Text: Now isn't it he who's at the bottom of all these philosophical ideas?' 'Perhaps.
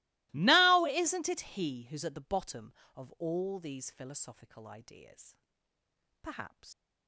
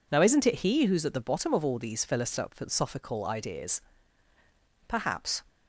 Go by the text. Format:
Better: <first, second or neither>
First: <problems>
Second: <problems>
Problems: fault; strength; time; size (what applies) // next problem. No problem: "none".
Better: second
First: starts louder than the rest; strong; until 1.3 s; 22.5 dB // leaves "Perhaps" unfinished; at 6.7 s; 105 ms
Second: none